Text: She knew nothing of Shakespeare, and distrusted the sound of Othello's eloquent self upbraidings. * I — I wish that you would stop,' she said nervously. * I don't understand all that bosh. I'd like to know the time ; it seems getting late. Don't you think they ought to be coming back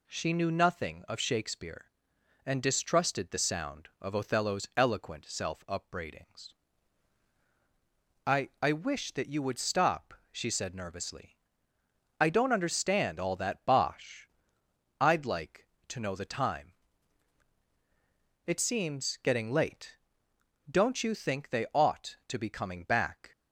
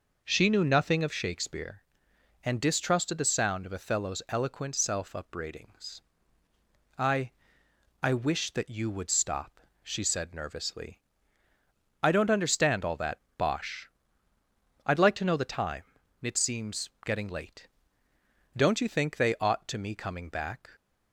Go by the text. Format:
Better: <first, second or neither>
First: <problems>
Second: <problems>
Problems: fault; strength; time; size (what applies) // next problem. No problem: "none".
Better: first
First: none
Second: pauses between "that" and "bosh"; slight; at 13.1 s; 0.18 s long // pauses between "seems" and "getting"; slight; at 16.8 s; 0.16 s long // says "me" for "be"; at 19.7 s